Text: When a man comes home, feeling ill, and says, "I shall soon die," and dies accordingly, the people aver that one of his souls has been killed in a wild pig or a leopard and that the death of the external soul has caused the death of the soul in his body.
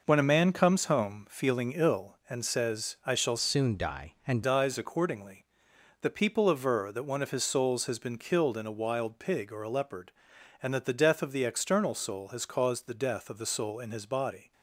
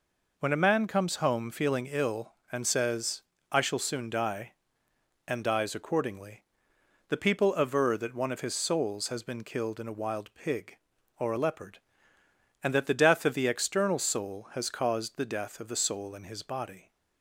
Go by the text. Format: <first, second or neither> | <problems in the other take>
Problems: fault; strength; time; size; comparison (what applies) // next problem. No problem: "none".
second | changes voice from "soon" to "and"; from 3.3 to 4.4 s; 1.1 s long